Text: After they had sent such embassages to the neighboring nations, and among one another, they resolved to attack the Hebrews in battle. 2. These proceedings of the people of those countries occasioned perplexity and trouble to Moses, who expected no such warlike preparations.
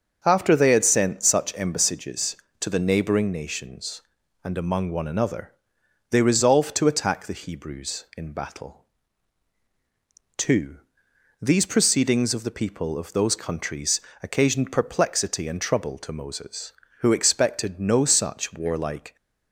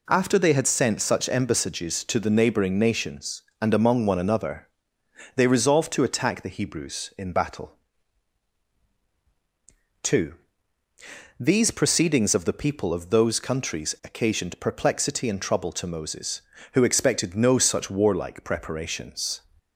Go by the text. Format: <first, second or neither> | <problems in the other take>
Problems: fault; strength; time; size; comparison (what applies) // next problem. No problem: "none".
second | starts louder than the rest; until 1.2 s; 6.5 dB // pauses between "countries" and "occasioned"; slight; at 13.9 s; 0.24 s long // stops before "preparations"; at 19.1 s